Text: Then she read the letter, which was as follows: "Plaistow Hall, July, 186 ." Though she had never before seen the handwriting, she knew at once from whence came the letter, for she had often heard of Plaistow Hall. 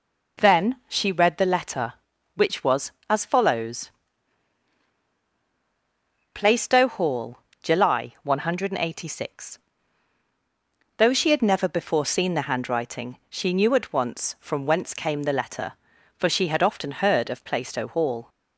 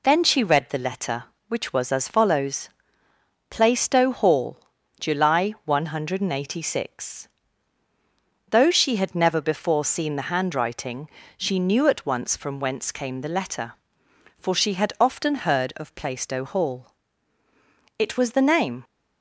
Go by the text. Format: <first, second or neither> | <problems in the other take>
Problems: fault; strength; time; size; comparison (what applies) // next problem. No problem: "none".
first | goes on to say "It was the name"; noticeable; from 17.9 s on; 0.86 s long